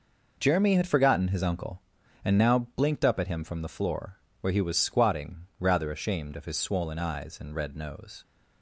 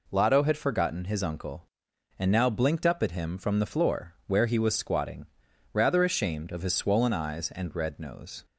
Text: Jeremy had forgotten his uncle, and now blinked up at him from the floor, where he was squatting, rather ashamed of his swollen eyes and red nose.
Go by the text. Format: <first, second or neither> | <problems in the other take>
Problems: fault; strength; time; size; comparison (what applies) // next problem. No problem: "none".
first | says "Lotto" for "Jeremy"; at 0.1 s